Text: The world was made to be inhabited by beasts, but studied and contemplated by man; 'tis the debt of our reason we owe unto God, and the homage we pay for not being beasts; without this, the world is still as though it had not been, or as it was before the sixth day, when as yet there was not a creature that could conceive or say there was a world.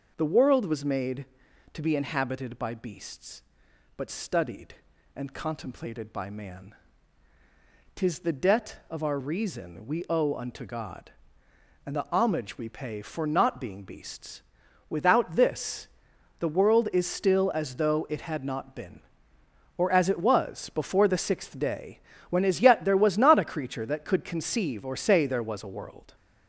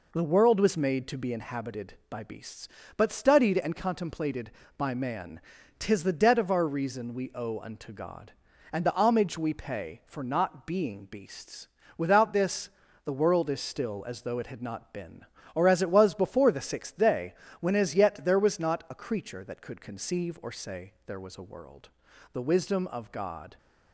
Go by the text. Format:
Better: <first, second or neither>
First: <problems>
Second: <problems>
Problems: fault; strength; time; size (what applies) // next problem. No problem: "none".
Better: first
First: none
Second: goes on to say "The wisdom of God"; noticeable; from 22.3 s on; 1.2 s long